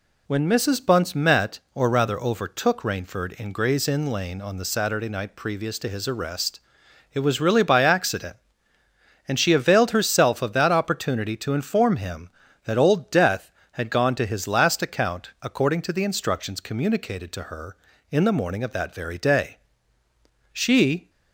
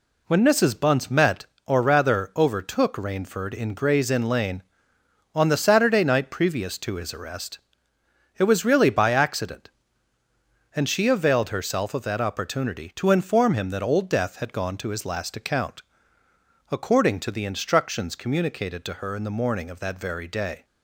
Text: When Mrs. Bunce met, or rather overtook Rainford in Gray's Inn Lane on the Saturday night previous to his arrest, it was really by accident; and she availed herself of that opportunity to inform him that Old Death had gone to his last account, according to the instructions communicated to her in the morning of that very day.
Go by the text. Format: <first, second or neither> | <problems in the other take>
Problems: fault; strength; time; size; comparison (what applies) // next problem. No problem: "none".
second | goes on to say "She"; from 20.5 s on; 0.58 s long